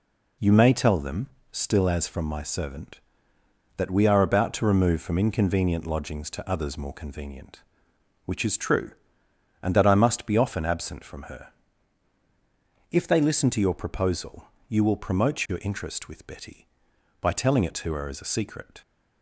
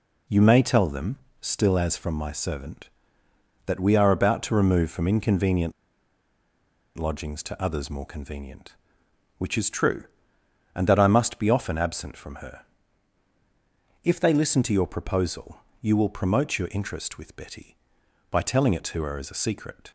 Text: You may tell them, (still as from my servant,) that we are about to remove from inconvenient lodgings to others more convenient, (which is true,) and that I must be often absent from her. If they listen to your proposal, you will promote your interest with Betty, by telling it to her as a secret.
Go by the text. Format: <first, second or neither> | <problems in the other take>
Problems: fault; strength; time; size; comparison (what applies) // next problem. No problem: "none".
first | pauses between "inconvenient" and "lodgings"; strong; at 5.7 s; 1.2 s long